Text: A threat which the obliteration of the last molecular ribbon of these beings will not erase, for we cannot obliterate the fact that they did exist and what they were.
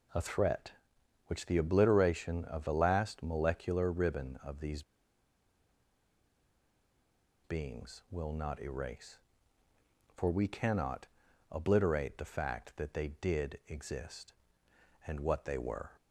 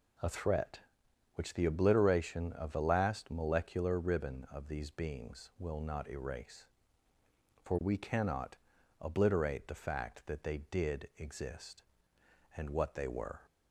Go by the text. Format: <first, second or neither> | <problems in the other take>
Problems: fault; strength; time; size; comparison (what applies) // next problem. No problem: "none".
second | pauses between "these" and "beings"; strong; at 4.8 s; 2.6 s long // pauses between "cannot" and "obliterate"; at 11.0 s; 0.44 s long; also in the second